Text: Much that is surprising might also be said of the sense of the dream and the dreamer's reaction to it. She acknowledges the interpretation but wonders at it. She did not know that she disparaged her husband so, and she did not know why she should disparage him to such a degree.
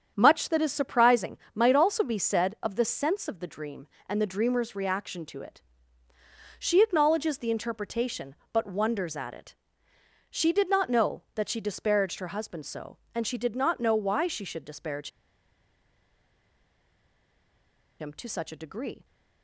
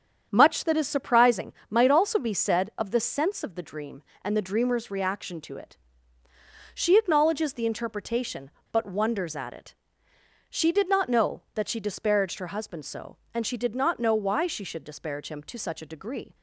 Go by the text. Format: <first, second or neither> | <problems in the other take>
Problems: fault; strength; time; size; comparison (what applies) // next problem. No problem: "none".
second | starts louder than the rest; strong; until 1.1 s; 8 dB; strong in the second // pauses between "surprising" and "might"; slight; at 1.3 s; 0.16 s long; slight in the second // pauses between "disparage" and "him"; strong; at 15.0 s; 2.9 s long